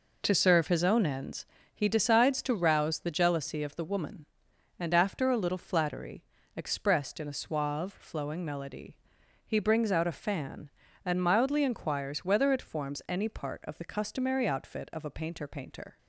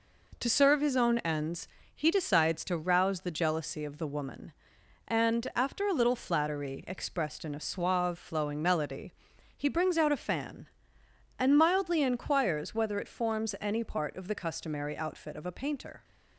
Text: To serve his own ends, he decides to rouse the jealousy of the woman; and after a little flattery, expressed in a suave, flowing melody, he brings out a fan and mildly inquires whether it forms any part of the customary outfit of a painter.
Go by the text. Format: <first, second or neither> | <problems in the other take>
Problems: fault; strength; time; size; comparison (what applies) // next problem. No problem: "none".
second | says "painter" twice; at 15.4 s